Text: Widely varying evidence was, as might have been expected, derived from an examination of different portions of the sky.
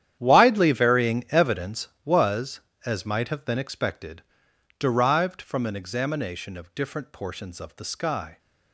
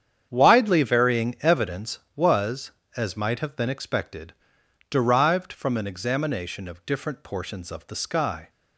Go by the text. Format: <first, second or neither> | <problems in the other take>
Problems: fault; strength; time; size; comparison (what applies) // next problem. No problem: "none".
second | gets quieter; strong; throughout; 15.5 dB // starts louder than the rest; strong; until 1.2 s; 10 dB; strong in the second